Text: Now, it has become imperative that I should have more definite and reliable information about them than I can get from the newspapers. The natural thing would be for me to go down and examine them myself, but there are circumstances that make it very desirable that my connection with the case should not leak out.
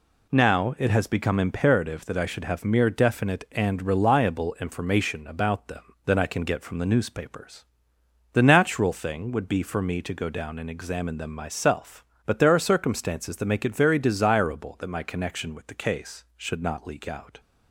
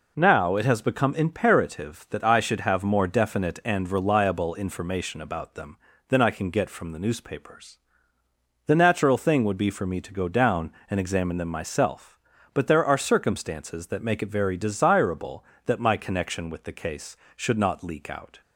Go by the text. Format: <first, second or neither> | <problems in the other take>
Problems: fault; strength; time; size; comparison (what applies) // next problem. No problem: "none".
second | says "mere" for "more"; at 2.6 s